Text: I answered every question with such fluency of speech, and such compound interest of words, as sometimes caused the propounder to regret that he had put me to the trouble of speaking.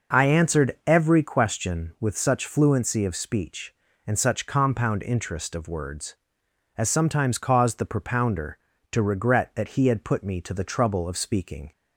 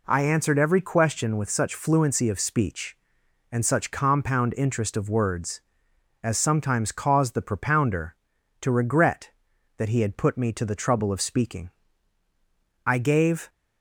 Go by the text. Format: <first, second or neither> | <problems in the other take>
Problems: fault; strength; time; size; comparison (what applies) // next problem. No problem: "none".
first | goes on to say "I gave"; noticeable; from 12.8 s on; 0.64 s long